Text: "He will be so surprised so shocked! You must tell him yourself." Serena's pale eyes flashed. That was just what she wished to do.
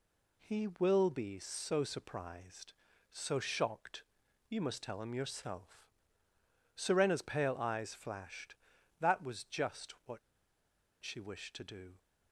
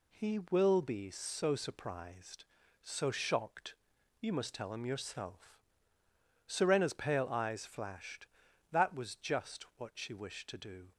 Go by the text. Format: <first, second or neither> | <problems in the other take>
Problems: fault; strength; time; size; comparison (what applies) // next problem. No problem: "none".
second | pauses between "just" and "what"; slight; at 9.9 s; 0.16 s long; slight in the second // pauses between "what" and "she"; noticeable; at 10.1 s; 0.84 s long